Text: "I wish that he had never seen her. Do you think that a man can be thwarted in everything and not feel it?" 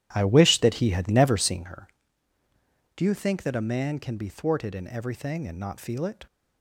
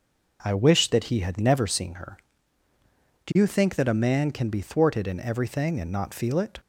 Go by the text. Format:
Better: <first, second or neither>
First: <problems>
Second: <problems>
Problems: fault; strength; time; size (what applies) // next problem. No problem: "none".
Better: second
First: starts louder than the rest; strong; until 1.8 s; 11.5 dB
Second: none